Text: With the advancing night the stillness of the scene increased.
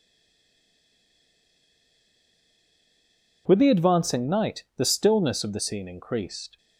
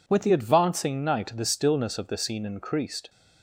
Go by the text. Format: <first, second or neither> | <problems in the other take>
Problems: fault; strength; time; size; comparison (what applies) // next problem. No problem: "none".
second | stays silent before the first word; strong; until 3.4 s; 3.4 s long